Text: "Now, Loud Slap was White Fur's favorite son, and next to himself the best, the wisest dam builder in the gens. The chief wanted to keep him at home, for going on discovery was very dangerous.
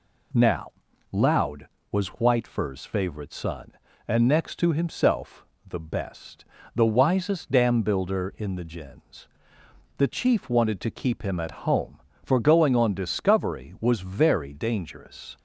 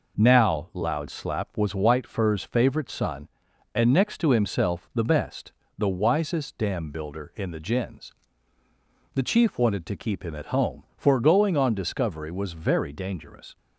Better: second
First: skips "Slap"; at 1.7 s // pauses between "himself" and "the"; slight; at 5.4 s; 0.22 s long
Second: none

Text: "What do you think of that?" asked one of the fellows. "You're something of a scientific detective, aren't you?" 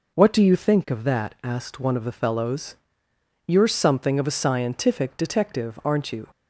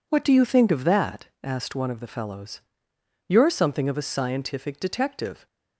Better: first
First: none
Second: stops before "aren't you"; at 5.4 s

